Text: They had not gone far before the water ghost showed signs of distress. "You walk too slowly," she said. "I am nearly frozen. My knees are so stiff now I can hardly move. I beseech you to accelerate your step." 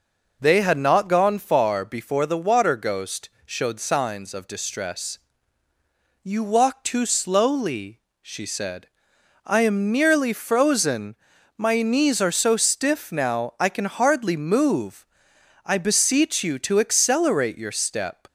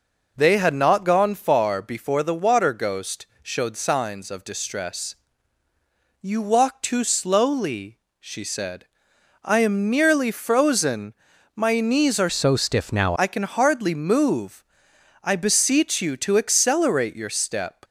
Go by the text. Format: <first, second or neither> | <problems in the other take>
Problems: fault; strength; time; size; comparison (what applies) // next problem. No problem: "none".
first | pauses between "ghost" and "showed"; slight; at 3.2 s; 0.16 s long; slight in the first // changes voice from "so" to "now"; from 12.3 to 13.1 s; 0.8 s long